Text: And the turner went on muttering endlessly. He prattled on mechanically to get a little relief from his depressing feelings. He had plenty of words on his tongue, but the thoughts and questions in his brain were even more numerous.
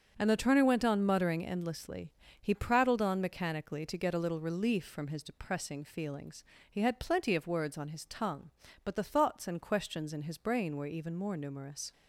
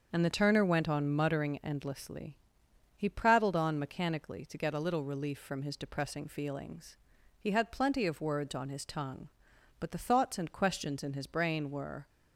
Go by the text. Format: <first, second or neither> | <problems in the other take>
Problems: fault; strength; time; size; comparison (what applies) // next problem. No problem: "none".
first | starts louder than the rest; until 1.1 s; 6.5 dB; strong in the first // stops before "even more numerous"; at 12.0 s